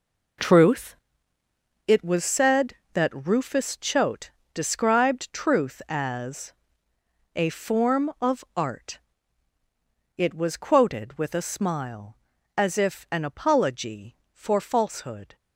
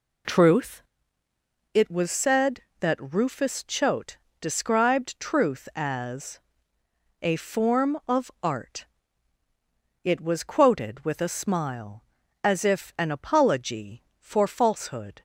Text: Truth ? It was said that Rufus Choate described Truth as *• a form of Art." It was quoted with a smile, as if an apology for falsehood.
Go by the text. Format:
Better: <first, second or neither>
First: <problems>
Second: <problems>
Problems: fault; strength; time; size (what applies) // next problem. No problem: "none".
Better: second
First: gets quieter; strong; throughout; 10 dB // pauses between "Choate" and "described"; slight; at 4.3 s; 0.22 s long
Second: pauses between "Choate" and "described"; slight; at 4.1 s; 0.22 s long